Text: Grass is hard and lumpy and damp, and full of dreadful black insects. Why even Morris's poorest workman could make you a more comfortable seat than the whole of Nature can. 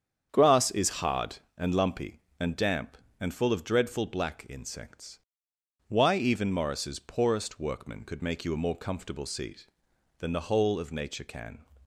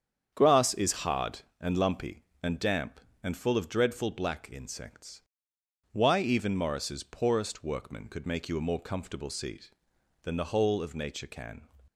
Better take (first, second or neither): neither